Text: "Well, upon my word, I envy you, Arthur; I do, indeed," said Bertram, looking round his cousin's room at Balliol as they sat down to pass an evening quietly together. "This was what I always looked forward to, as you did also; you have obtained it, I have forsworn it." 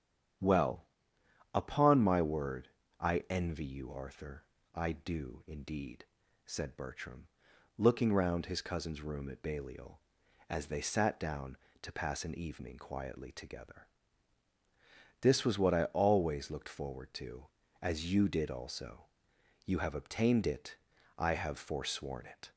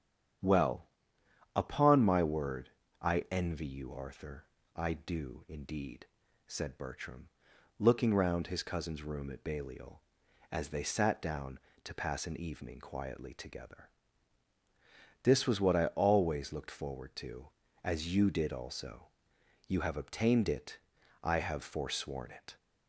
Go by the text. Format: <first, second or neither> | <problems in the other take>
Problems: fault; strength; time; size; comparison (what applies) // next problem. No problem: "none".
neither | starts louder than the rest; strong; the same in both